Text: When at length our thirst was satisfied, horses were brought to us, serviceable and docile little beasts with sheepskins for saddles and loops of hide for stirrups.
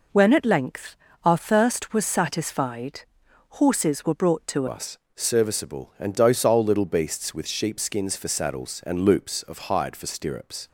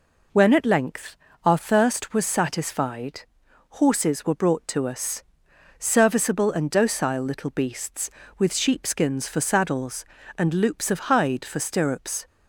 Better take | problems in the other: second | pauses between "length" and "our"; slight; at 0.9 s; 0.28 s long; slight in the second // changes voice at "us"; from 4.6 s on; 6.0 s long

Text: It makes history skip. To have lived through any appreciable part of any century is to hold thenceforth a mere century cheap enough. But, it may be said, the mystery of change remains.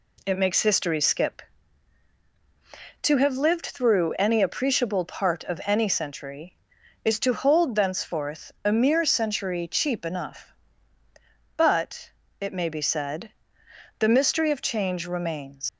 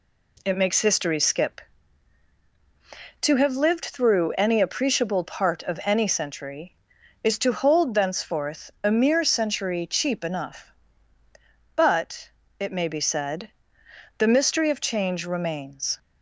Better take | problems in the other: second | leaves "remains" unfinished; at 15.6 s; 100 ms

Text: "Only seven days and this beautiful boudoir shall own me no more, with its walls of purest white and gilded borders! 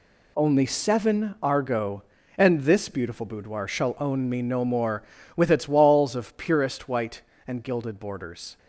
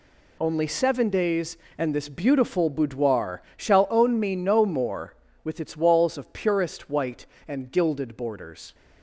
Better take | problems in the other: second | says "argo" for "days"; at 1.4 s

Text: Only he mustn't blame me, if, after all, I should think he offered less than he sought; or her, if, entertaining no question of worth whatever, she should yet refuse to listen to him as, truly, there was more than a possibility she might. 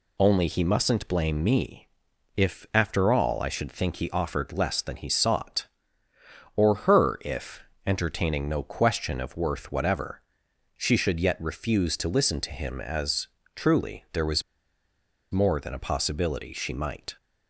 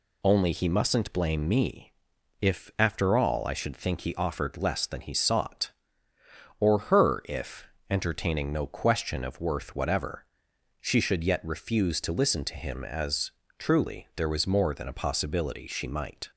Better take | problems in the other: second | pauses between "was" and "more"; noticeable; at 14.4 s; 0.90 s long

